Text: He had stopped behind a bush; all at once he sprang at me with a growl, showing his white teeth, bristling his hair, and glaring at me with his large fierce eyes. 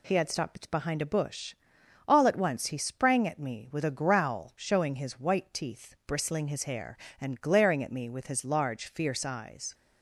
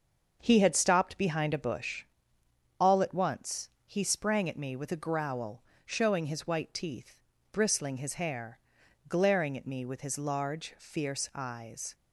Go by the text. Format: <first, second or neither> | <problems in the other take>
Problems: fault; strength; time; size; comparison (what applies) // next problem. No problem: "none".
first | starts louder than the rest; until 1.4 s; 6.5 dB // pauses between "once" and "he"; slight; at 3.6 s; 0.18 s long // skips "and"; at 8.8 s